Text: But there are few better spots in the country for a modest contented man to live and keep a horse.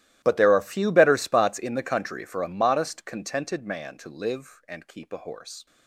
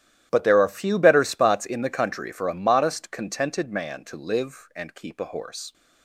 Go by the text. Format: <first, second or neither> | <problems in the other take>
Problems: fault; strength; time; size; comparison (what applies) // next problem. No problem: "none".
second | gets quieter; strong; throughout; 21.5 dB // starts louder than the rest; strong; until 1.2 s; 14.5 dB; strong in the second